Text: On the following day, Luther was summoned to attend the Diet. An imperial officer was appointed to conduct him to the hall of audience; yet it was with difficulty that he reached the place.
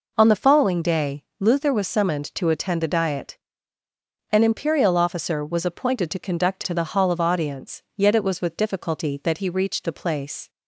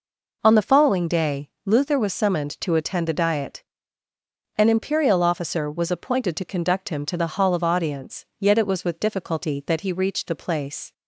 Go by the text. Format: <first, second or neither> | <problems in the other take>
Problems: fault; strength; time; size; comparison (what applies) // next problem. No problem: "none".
second | skips "him"; at 6.6 s